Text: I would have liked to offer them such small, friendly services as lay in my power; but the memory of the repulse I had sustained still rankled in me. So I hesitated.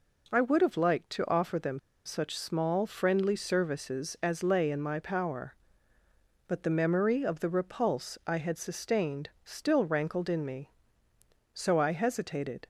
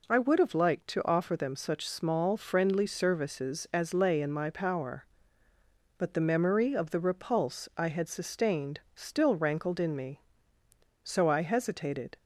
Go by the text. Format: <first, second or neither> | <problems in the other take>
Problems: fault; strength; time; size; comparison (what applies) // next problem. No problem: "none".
second | pauses between "them" and "such"; slight; at 1.7 s; 0.26 s long